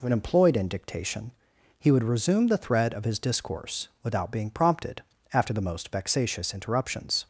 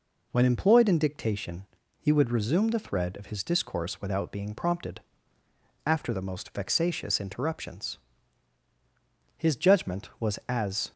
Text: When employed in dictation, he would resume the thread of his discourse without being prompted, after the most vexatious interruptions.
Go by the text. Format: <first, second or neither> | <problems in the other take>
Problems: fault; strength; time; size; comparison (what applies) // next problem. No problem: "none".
first | goes on to say "His judgment was as"; from 9.3 s on; 1.5 s long